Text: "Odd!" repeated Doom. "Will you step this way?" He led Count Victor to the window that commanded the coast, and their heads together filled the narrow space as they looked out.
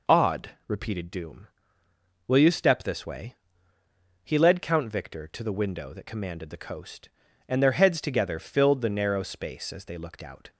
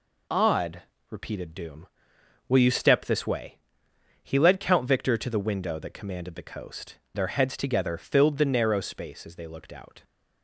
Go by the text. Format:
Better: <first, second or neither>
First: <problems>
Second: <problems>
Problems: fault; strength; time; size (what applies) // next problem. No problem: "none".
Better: first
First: none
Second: skips "and"; at 7.0 s